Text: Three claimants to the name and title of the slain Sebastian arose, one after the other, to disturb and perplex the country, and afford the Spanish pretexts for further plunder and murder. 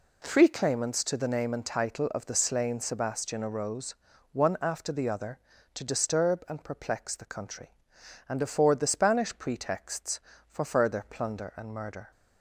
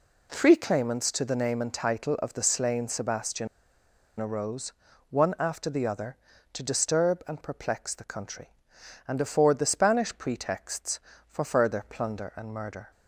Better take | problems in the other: first | pauses between "Sebastian" and "arose"; noticeable; at 3.4 s; 0.72 s long

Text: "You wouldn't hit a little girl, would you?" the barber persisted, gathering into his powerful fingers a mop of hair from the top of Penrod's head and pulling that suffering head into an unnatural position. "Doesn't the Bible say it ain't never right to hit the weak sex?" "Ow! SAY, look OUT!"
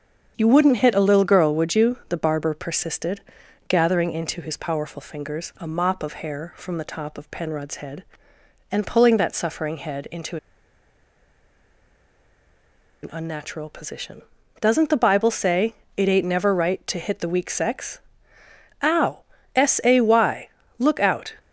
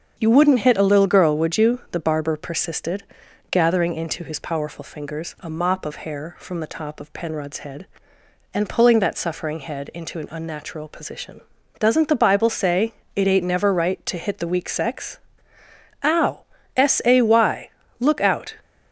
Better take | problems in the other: second | starts louder than the rest; strong; until 1.3 s; 7 dB; also in the second // pauses between "into" and "an"; strong; at 10.3 s; 2.6 s long // pauses between "say" and "it"; slight; at 15.7 s; 0.20 s long; slight in the second

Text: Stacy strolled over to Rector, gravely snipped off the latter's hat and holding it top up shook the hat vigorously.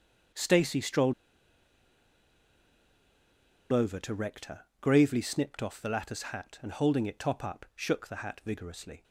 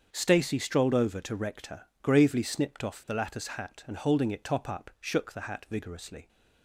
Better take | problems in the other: second | starts louder than the rest; until 3.9 s; 7 dB; strong in the second // pauses between "strolled" and "over"; strong; at 1.1 s; 2.5 s long

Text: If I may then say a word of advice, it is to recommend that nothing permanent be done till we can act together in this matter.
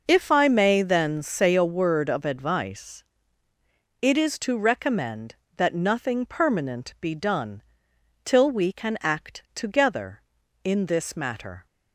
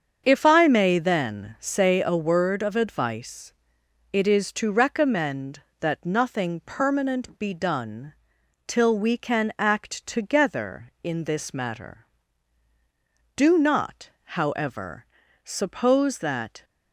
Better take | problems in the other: first | starts louder than the rest; until 1.2 s; 7 dB // pauses between "done" and "till"; noticeable; at 8.1 s; 0.54 s long; noticeable in the first // goes on to say "Do not however suppose that"; strong; from 13.3 s on; 3.2 s long

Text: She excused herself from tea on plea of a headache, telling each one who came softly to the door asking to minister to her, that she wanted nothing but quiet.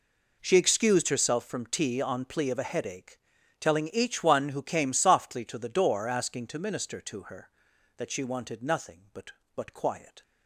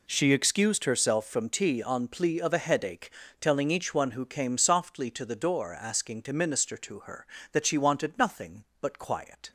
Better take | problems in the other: second | says "but" twice; at 9.5 s

